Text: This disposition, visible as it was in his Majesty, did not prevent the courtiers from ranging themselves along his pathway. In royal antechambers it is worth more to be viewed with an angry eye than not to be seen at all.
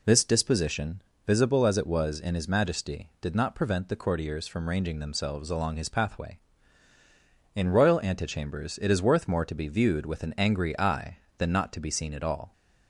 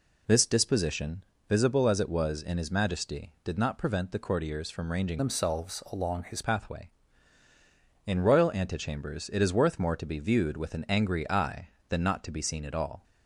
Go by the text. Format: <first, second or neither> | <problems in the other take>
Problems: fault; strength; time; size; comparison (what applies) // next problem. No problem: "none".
first | changes voice from "themselves" to "his"; from 5.1 to 6.4 s; 1.3 s long